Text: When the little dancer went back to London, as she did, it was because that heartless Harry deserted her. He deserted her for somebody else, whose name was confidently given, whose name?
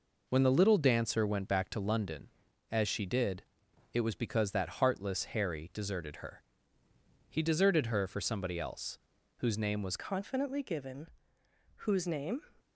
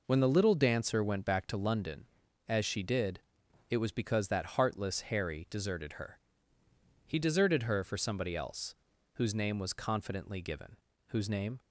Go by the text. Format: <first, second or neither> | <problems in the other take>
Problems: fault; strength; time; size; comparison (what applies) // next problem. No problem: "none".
second | changes voice at "confidently"; from 9.9 s on; 2.5 s long